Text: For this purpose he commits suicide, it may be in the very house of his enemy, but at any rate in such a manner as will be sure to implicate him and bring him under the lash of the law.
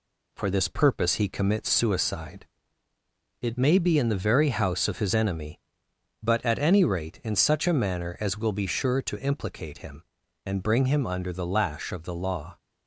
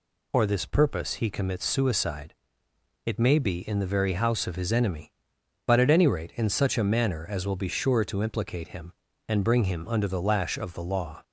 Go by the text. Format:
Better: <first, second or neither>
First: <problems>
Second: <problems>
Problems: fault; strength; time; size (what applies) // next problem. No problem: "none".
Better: second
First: gets quieter; slight; throughout; 2 dB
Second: none